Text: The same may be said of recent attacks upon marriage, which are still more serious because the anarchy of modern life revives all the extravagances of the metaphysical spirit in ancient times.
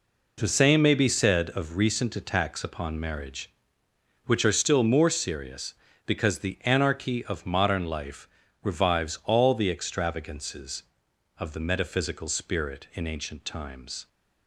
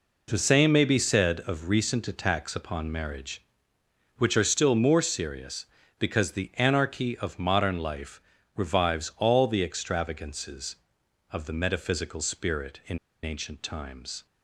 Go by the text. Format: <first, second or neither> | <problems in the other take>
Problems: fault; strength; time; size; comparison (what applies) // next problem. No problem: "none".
first | pauses between "life" and "revives"; slight; at 8.2 s; 0.34 s long; slight in the first // pauses between "in" and "ancient"; slight; at 12.9 s; 0.25 s long